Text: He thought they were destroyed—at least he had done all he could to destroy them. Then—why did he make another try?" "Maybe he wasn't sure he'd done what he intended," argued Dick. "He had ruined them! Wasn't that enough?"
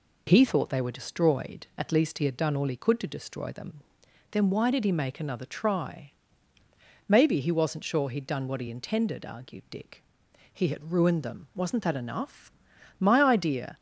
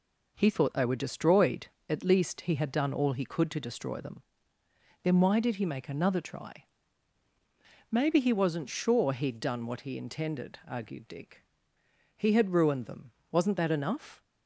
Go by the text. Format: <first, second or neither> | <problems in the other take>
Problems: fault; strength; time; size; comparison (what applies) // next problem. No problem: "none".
second | goes on to say "My idea"; noticeable; from 12.9 s on; 0.80 s long